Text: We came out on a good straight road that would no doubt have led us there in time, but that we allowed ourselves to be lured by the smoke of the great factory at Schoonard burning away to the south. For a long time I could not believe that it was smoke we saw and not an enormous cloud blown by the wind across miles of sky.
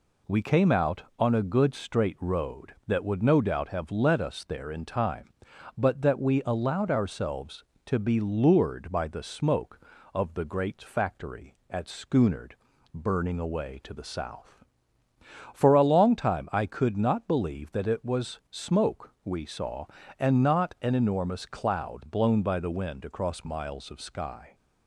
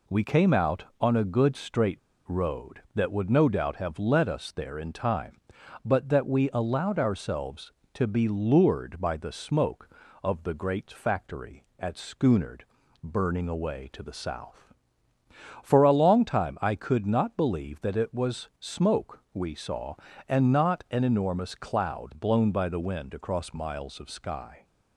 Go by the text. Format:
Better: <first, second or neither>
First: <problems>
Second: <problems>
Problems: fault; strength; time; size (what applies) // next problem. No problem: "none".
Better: first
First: pauses between "Schoonard" and "burning"; at 12.5 s; 0.42 s long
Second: pauses between "straight" and "road"; slight; at 1.9 s; 0.27 s long // pauses between "Schoonard" and "burning"; at 12.6 s; 0.42 s long